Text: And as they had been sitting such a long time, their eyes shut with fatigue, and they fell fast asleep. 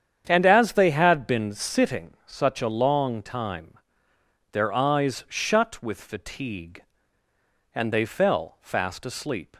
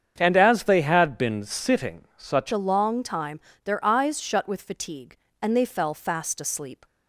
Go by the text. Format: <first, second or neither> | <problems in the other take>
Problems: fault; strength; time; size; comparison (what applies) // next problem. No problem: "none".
first | starts louder than the rest; strong; until 1.1 s; 7.5 dB; strong in the first // changes voice at "a"; from 2.5 s on; 4.3 s long